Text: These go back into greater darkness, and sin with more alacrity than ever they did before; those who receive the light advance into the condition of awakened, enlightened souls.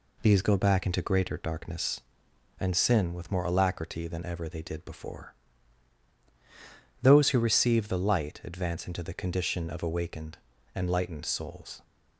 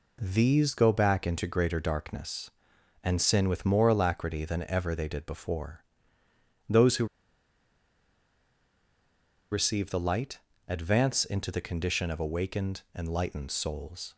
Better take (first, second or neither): first